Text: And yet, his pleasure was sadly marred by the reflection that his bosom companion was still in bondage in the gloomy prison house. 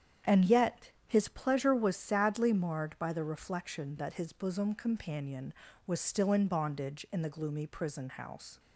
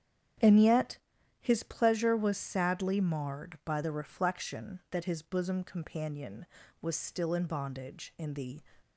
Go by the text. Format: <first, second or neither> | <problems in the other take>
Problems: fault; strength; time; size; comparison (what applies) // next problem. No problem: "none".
first | starts louder than the rest; strong; until 1.8 s; 8.5 dB; strong in the first // stops before "gloomy prison house"; at 8.8 s